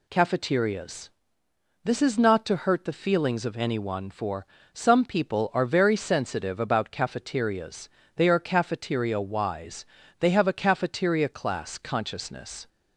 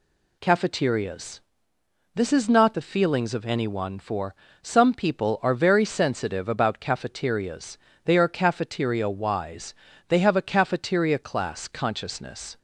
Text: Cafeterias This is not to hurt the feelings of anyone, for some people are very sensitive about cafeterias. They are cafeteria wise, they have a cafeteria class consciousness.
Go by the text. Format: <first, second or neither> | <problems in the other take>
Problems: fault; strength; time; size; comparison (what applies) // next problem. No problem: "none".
first | pauses between "Cafeterias" and "This"; noticeable; at 1.3 s; 0.74 s long; noticeable in the first // skips "to hurt"; at 2.7 s // pauses between "for" and "some"; slight; at 4.3 s; 0.28 s long; slight in the first